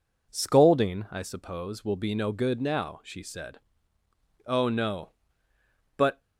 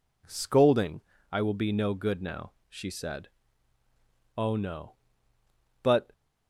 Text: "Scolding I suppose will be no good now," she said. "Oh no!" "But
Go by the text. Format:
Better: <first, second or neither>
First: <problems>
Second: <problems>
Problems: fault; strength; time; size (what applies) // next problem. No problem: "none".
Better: first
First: none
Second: pauses between "Scolding" and "I"; slight; at 1.0 s; 0.28 s long // skips "suppose"; at 1.4 s